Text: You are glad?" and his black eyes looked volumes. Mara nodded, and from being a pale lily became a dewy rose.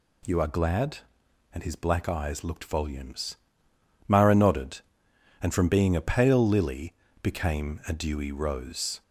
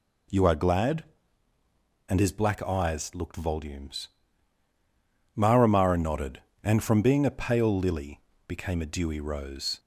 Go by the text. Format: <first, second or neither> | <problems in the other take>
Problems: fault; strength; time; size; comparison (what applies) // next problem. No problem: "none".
first | says "Mara" twice; at 5.6 s // pauses between "lily" and "became"; slight; at 8.1 s; 0.28 s long; slight in the first